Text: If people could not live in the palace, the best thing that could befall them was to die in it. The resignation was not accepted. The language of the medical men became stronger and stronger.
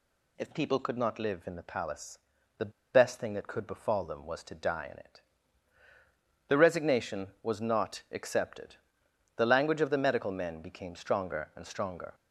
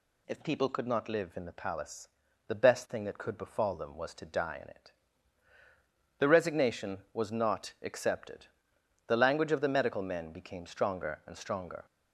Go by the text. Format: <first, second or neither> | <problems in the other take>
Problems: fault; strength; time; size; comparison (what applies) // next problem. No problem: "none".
second | pauses between "the" and "best"; slight; at 2.7 s; 0.22 s long